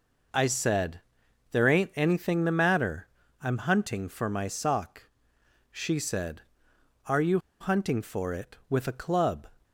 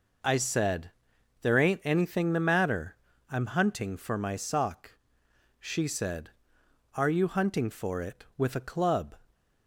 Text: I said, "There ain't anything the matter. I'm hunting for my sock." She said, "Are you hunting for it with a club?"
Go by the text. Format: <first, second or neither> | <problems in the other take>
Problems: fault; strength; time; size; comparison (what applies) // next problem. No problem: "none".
second | pauses between "you" and "hunting"; slight; at 7.3 s; 0.22 s long